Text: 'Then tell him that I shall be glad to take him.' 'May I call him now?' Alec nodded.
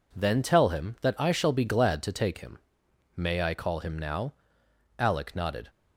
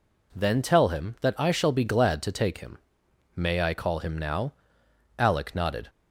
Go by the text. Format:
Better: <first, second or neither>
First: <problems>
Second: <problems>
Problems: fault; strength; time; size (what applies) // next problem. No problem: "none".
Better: second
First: gets quieter; throughout; 6.5 dB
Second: none